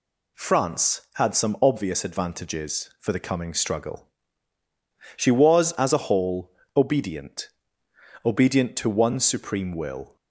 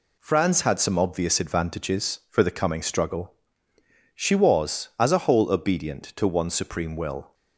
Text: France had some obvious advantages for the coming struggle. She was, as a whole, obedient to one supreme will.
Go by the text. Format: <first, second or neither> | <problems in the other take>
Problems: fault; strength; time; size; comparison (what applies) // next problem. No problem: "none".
second | says "obedient" twice; at 8.2 s